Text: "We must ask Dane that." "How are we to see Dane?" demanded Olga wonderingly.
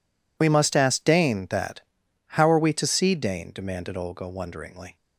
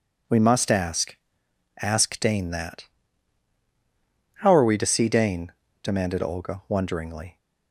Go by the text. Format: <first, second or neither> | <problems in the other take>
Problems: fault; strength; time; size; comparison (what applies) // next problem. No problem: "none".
first | says "ask" twice; at 1.8 s